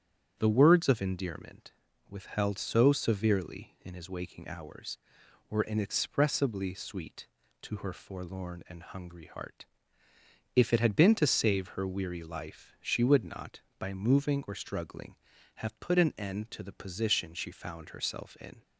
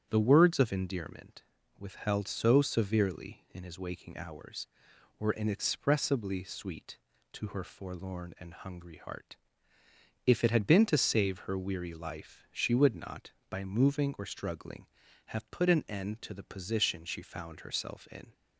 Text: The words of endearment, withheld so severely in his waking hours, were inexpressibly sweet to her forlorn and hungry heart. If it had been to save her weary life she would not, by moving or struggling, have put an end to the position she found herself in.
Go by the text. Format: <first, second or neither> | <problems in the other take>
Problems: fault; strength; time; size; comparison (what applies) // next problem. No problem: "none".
neither | starts louder than the rest; strong; the same in both